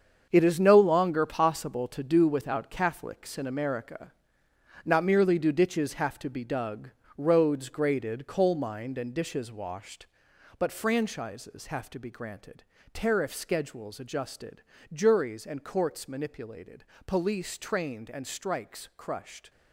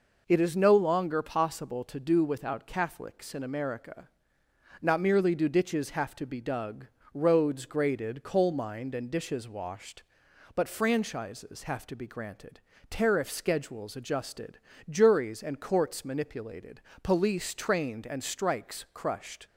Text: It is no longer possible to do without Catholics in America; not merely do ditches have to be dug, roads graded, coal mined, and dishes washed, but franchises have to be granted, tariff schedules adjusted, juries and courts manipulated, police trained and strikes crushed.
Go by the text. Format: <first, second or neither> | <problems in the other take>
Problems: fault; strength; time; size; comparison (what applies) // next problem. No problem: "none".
second | gets quieter; strong; throughout; 10 dB